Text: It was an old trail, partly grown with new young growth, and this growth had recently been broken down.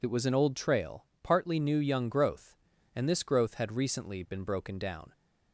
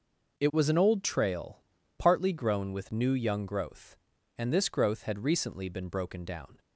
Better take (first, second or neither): second